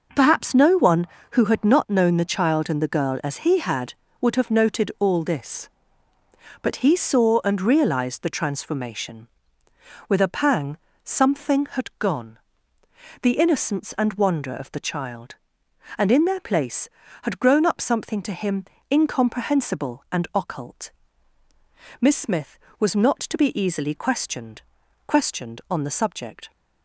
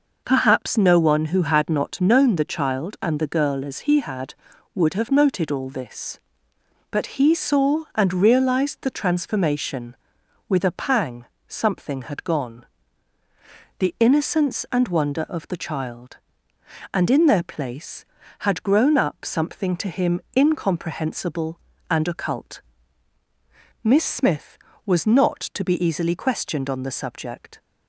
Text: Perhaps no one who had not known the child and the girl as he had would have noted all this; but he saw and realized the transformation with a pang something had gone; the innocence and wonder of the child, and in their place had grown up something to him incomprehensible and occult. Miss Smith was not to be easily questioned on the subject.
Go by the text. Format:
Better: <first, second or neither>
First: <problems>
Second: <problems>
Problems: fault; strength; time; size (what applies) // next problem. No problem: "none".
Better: second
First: pauses between "pang" and "something"; slight; at 10.7 s; 0.28 s long // pauses between "him" and "incomprehensible"; slight; at 18.6 s; 0.26 s long // says "questioned" twice; at 25.0 s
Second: pauses between "pang" and "something"; slight; at 11.2 s; 0.24 s long // pauses between "him" and "incomprehensible"; slight; at 20.2 s; 0.16 s long